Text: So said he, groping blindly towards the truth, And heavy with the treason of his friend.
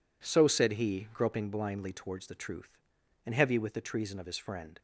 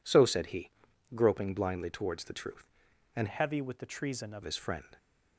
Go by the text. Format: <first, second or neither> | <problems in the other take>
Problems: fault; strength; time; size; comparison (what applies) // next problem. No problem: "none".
first | changes voice from "heavy" to "of"; from 3.2 to 4.4 s; 1.2 s long